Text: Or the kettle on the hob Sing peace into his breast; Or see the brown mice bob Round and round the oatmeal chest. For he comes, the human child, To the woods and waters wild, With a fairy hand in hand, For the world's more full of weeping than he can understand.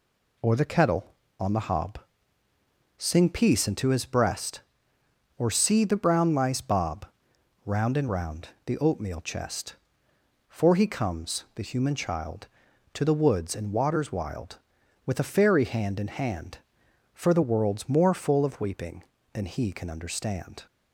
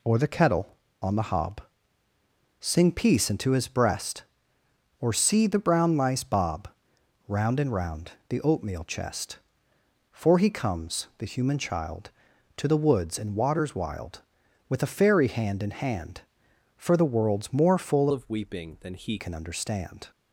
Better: first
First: pauses between "hob" and "Sing"; noticeable; at 1.9 s; 0.98 s long // pauses between "bob" and "Round"; noticeable; at 7.0 s; 0.60 s long // pauses between "round" and "the"; slight; at 8.4 s; 0.18 s long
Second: pauses between "hob" and "Sing"; noticeable; at 1.6 s; 0.98 s long // pauses between "bob" and "Round"; noticeable; at 6.6 s; 0.60 s long // pauses between "round" and "the"; slight; at 8.1 s; 0.18 s long // changes voice from "of" to "he"; from 18.1 to 19.1 s; 1.0 s long

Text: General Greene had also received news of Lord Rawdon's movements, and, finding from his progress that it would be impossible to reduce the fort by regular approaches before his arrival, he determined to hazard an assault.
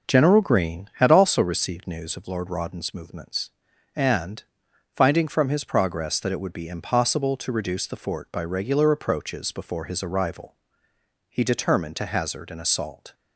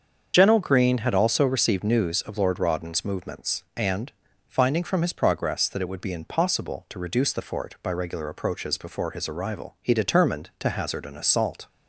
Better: first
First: none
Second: loses the start of "General"; at 0.3 s; 50 ms // starts louder than the rest; until 1.3 s; 7 dB

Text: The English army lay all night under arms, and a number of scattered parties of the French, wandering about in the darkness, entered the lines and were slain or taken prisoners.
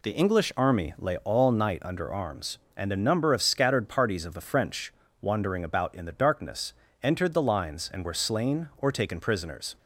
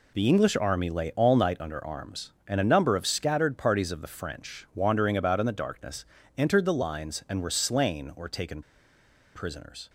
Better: first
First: none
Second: pauses between "taken" and "prisoners"; noticeable; at 8.6 s; 0.72 s long

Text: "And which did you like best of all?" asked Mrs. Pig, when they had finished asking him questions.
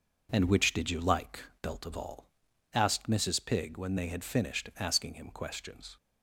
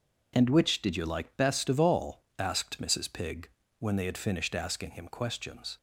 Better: second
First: says "belt" for "best"; at 1.6 s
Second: none

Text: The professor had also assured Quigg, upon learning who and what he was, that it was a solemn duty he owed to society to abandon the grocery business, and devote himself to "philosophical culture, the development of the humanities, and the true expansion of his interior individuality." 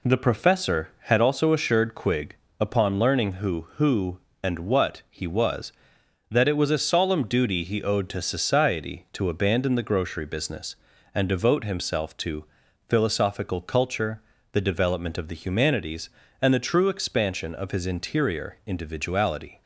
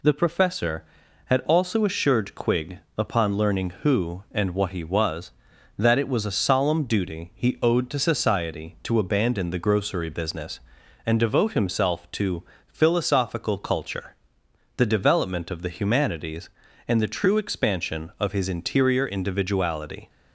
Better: second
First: says "who" twice; at 3.7 s // pauses between "to" and "philosophical"; at 12.4 s; 0.42 s long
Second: pauses between "to" and "philosophical"; slight; at 12.4 s; 0.24 s long

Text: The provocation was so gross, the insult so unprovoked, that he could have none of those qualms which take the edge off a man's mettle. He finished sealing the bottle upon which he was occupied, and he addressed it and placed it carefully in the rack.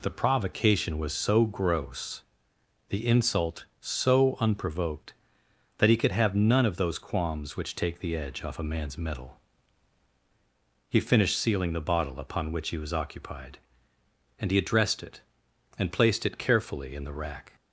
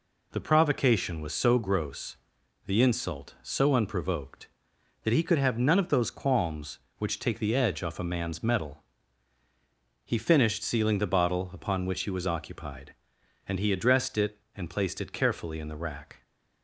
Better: neither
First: none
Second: none

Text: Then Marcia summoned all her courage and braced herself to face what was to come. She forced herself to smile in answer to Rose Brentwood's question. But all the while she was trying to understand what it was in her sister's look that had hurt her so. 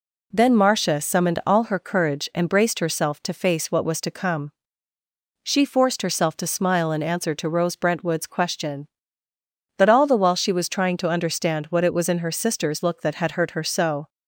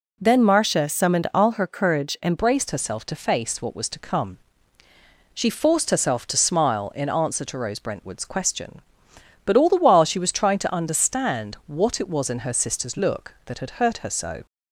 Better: first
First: none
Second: changes voice at "braced"; from 2.3 s on; 12.1 s long

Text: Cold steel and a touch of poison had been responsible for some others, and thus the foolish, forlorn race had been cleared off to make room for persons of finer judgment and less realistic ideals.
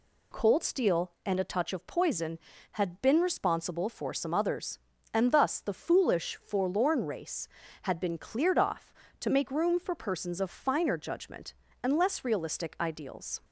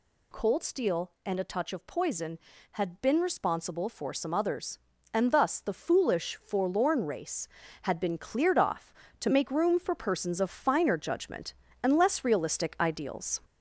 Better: first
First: none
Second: gets louder; throughout; 3.5 dB

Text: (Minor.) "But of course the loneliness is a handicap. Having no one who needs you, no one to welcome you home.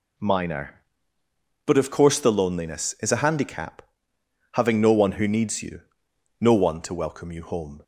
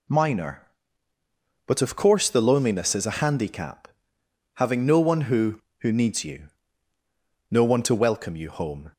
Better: first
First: none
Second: says "who" twice; at 5.8 s

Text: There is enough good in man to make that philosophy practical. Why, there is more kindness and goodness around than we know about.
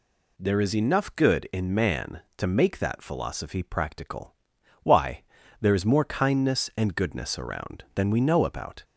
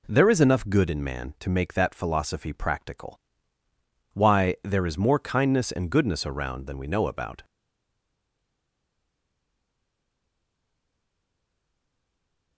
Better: first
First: none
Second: stays silent after the last word; strong; from 7.4 s on; 5.1 s long

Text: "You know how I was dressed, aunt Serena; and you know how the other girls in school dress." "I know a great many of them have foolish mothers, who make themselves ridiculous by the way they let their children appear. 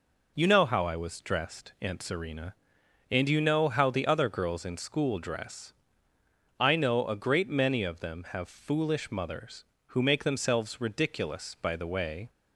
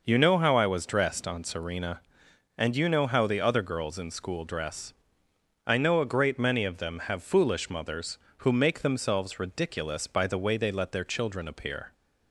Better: second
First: stops before "they let their children appear"; at 12.2 s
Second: none

